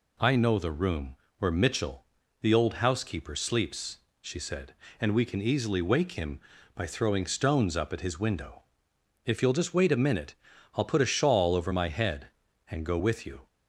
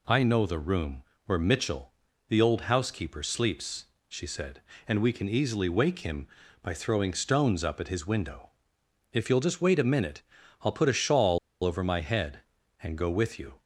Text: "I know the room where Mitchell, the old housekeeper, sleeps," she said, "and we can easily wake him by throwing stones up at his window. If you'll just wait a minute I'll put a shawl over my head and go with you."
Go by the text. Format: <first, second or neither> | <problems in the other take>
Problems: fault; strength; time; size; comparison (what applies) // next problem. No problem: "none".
first | pauses between "room" and "where"; slight; at 1.0 s; 0.22 s long; slight in the first // pauses between "minute" and "I'll"; at 10.2 s; 0.40 s long; also in the first // pauses between "shawl" and "over"; slight; at 11.3 s; 0.25 s long